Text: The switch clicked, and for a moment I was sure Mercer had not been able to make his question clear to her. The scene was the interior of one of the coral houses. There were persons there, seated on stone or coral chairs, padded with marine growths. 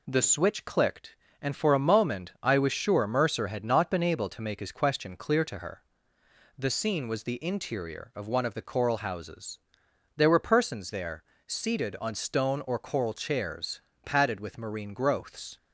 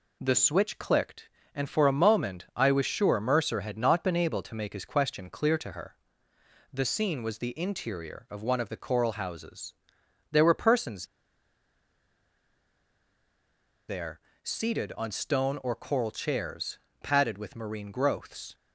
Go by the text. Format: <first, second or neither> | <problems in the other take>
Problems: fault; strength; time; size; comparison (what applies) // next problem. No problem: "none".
first | pauses between "persons" and "there"; strong; at 11.0 s; 2.8 s long